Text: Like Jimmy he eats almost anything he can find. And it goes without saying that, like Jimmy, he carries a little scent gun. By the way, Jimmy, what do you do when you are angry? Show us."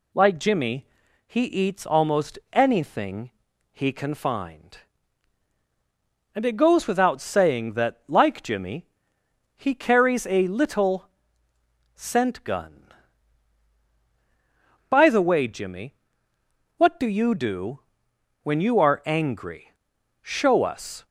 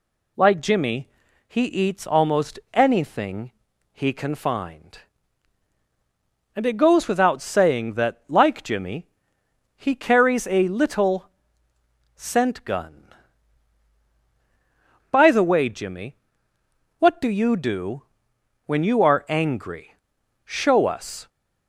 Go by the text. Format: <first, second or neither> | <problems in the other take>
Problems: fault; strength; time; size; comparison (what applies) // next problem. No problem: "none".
neither | pauses between "Jimmy" and "he"; the same in both // pauses between "anything" and "he"; the same in both // pauses between "little" and "scent"; noticeable; the same in both // pauses between "do" and "when"; noticeable; the same in both